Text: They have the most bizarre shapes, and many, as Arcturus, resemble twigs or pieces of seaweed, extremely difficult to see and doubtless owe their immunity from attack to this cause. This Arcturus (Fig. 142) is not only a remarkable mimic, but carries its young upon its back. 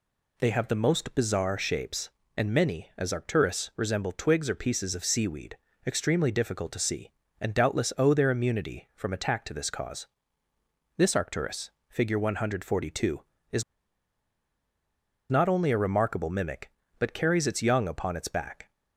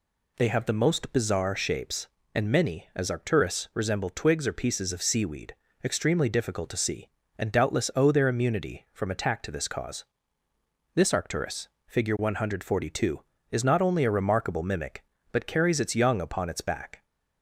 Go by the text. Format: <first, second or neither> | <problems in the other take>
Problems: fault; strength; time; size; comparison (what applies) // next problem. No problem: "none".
second | pauses between "is" and "not"; strong; at 13.6 s; 1.6 s long